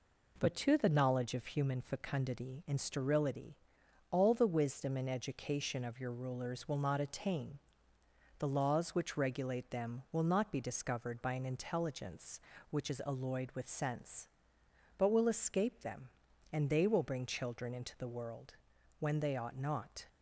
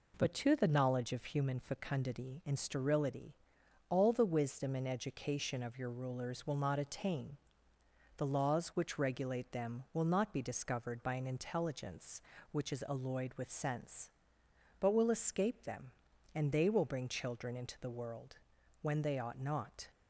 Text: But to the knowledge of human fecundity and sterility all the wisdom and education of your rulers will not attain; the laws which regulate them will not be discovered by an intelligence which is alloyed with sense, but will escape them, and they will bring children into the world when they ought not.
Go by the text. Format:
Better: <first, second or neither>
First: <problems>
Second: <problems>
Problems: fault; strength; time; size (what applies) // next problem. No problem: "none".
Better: neither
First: pauses between "sterility" and "all"; noticeable; at 3.5 s; 0.52 s long // pauses between "world" and "when"; at 18.5 s; 0.44 s long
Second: pauses between "sterility" and "all"; noticeable; at 3.3 s; 0.52 s long // pauses between "world" and "when"; at 18.3 s; 0.44 s long